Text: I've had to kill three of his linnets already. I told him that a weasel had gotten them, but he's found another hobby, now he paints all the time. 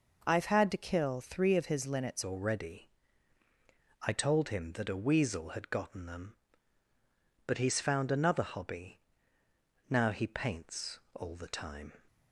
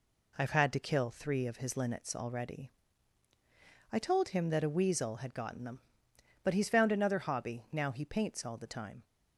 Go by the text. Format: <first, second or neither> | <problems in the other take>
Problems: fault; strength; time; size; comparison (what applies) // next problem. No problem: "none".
second | changes voice at "already"; from 2.2 s on; 9.7 s long // pauses between "paints" and "all"; slight; at 10.9 s; 0.16 s long